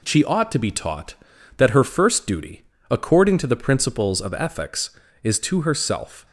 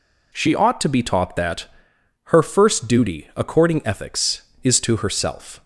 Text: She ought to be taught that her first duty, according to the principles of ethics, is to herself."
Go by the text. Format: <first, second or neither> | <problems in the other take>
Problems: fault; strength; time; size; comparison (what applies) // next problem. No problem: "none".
first | pauses between "that" and "her"; noticeable; at 1.6 s; 0.58 s long // skips "to the principles of"; at 3.8 s